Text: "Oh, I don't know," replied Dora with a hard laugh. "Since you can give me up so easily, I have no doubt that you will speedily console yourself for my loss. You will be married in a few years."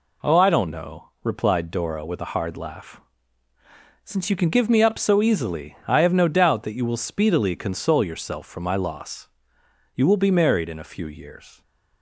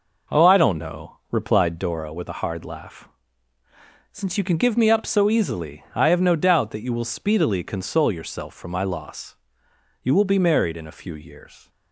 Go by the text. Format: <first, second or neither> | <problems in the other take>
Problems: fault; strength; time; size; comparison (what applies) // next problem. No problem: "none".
first | starts louder than the rest; noticeable; until 1.9 s; 5 dB